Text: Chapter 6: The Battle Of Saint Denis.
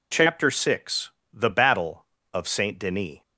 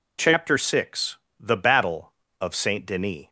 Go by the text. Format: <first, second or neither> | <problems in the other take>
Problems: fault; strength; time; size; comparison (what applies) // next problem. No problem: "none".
neither | none